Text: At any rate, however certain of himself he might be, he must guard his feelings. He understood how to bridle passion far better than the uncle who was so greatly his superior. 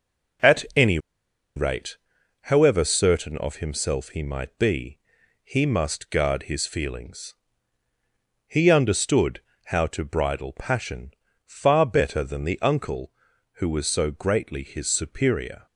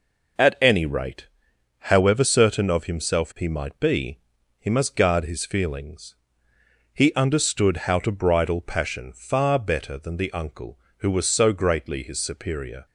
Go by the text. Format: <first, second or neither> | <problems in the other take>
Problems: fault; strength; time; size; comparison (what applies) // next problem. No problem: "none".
second | pauses between "any" and "rate"; noticeable; at 0.9 s; 0.57 s long // pauses between "understood" and "how"; slight; at 9.4 s; 0.24 s long // pauses between "passion" and "far"; slight; at 11.1 s; 0.32 s long